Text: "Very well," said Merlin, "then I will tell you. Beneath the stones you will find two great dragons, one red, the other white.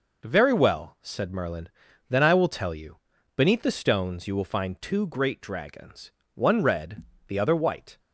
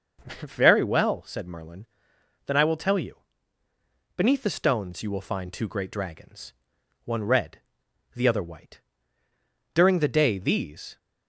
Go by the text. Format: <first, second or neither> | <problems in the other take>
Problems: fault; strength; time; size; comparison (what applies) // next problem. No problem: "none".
first | starts louder than the rest; noticeable; until 1.2 s; 6 dB // goes on to say "During the day these"; noticeable; from 9.7 s on; 1.2 s long